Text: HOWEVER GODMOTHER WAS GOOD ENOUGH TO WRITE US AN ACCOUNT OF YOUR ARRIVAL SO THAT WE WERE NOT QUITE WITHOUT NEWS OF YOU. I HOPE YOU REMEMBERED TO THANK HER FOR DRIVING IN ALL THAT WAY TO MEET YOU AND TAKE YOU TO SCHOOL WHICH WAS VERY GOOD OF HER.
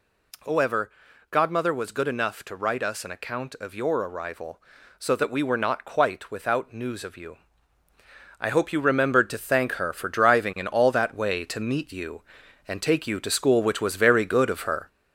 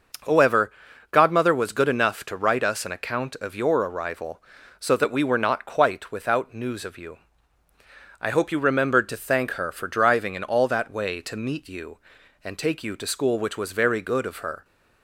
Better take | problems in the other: second | gets louder; noticeable; throughout; 4.5 dB // pauses between "HOWEVER" and "GODMOTHER"; at 0.9 s; 0.40 s long; also in the second

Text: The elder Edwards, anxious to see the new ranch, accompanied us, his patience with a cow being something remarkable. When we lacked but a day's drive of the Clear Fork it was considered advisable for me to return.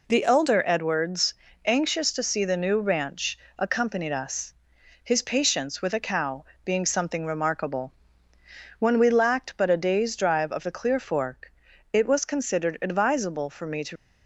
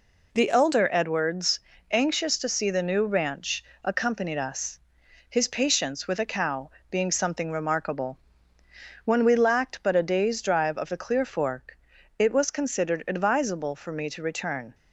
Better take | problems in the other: second | pauses between "cow" and "being"; slight; at 6.4 s; 0.18 s long; slight in the second // pauses between "Fork" and "it"; at 11.5 s; 0.40 s long; also in the second // stops before "return"; at 13.9 s

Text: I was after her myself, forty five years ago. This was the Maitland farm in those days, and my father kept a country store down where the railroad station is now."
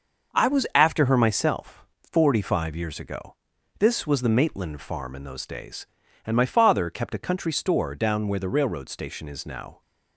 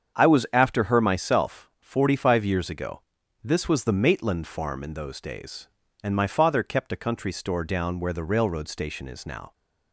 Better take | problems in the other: neither | starts louder than the rest; the same in both

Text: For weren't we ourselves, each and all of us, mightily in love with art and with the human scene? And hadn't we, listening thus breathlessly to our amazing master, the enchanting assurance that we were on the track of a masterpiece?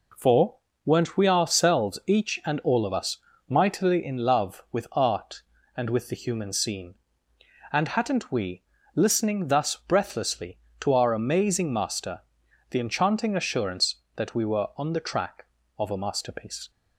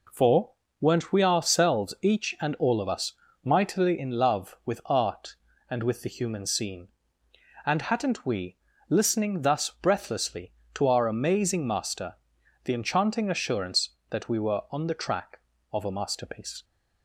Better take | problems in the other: neither | pauses between "For" and "weren't"; slight; the same in both

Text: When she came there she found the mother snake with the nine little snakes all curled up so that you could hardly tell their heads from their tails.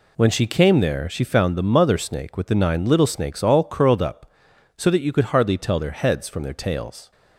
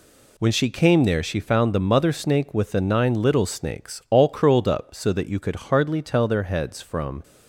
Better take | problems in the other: first | stops before "their tails"; at 7.2 s

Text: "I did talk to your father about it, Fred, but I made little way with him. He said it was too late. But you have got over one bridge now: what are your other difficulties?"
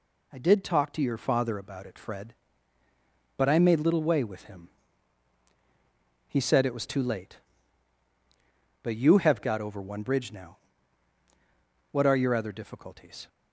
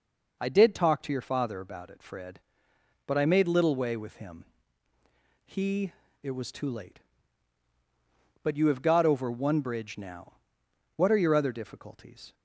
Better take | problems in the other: first | skips "said"; at 6.0 s

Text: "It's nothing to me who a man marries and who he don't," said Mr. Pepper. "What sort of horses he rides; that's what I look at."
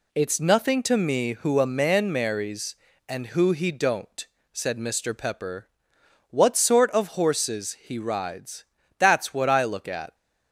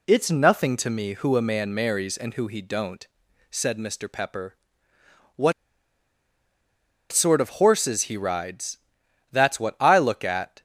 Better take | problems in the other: first | pauses between "What" and "sort"; strong; at 5.5 s; 1.5 s long

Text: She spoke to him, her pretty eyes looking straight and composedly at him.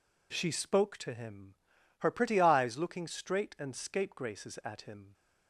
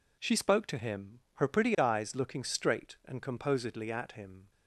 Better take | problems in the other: second | says "scapegraces" for "composedly"; at 3.7 s

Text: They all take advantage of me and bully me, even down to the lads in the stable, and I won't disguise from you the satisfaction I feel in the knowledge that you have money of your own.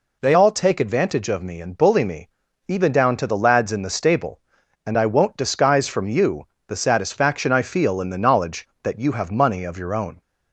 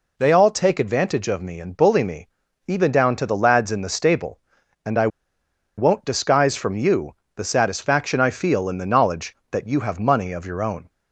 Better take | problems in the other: first | pauses between "I" and "won't"; noticeable; at 5.0 s; 0.69 s long // pauses between "you" and "the"; slight; at 7.1 s; 0.22 s long; slight in the first

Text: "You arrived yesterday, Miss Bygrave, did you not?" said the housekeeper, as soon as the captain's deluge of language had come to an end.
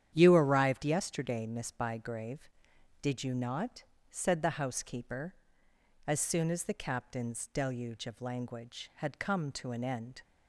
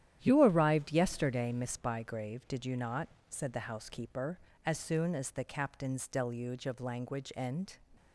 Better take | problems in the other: first | starts louder than the rest; strong; until 1.2 s; 11 dB; strong in the first // skips "had come to an"; at 7.3 s

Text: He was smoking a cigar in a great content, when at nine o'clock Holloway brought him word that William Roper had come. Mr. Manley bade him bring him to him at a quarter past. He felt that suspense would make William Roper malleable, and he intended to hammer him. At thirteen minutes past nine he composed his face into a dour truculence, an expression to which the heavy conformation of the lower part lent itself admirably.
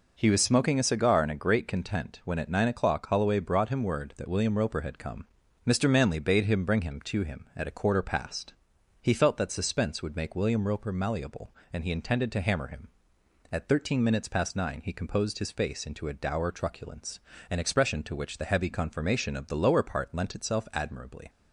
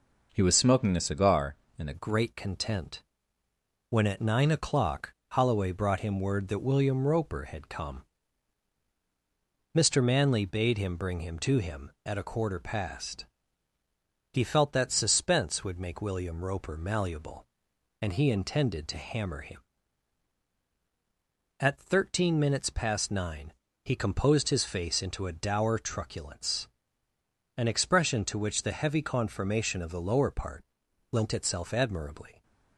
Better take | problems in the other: first | changes voice at "great"; from 1.9 s on; 30.5 s long // pauses between "o'clock" and "Holloway"; slight; at 5.1 s; 0.16 s long // pauses between "nine" and "he"; slight; at 23.5 s; 0.28 s long // pauses between "part" and "lent"; noticeable; at 30.6 s; 0.48 s long

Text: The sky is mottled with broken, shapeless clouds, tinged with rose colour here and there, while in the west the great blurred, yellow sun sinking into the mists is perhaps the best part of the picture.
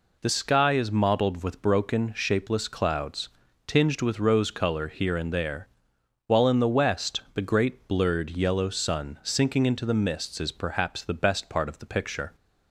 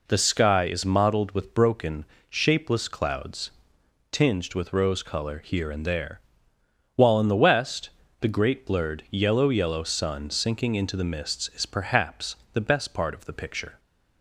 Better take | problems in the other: first | pauses between "west" and "the"; slight; at 7.8 s; 0.30 s long // says "yellow" twice; at 9.4 s // pauses between "perhaps" and "the"; slight; at 12.3 s; 0.16 s long

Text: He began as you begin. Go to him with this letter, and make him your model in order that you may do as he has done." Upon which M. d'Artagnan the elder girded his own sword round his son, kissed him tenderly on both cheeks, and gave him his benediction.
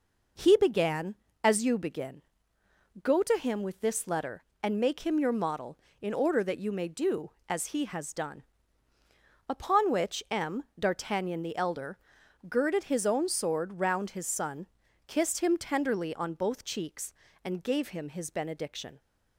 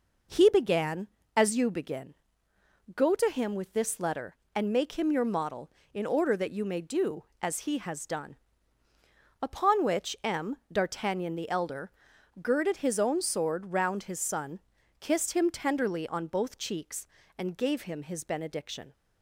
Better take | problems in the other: neither | pauses between "elder" and "girded"; noticeable; the same in both

